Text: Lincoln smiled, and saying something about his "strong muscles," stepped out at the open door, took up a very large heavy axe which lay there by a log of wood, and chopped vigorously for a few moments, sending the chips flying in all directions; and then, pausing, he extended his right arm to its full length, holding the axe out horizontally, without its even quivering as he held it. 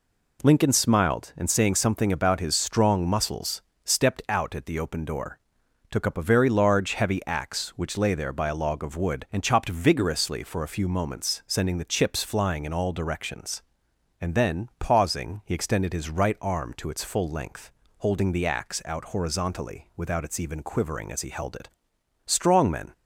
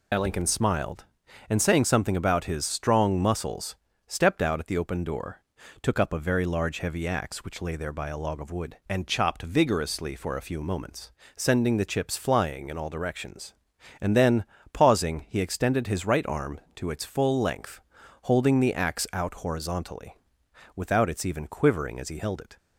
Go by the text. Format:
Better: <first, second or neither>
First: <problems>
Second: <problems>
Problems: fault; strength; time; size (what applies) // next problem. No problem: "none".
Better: second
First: goes on to say "Strong men"; noticeable; from 22.2 s on; 0.68 s long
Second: none